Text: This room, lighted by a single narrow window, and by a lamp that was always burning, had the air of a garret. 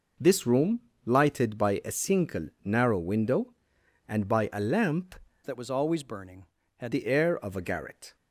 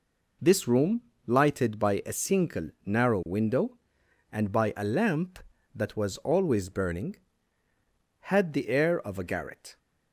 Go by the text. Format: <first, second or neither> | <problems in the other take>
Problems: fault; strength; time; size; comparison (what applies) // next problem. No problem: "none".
second | pauses between "single" and "narrow"; slight; at 2.4 s; 0.16 s long; slight in the second // changes voice from "that" to "had"; from 5.4 to 6.9 s; 1.5 s long